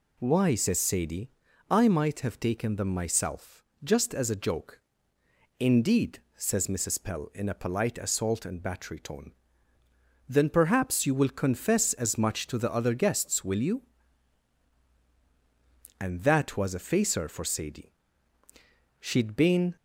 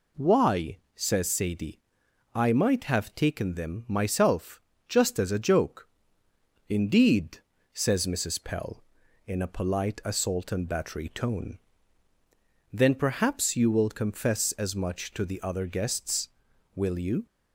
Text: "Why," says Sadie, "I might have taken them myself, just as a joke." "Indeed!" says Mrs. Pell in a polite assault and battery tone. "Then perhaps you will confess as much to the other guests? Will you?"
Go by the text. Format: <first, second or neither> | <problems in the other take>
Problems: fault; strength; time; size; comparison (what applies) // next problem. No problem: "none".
second | goes on to say "And that was a facer for Sadie She'd been"; strong; from 15.9 s on; 3.7 s long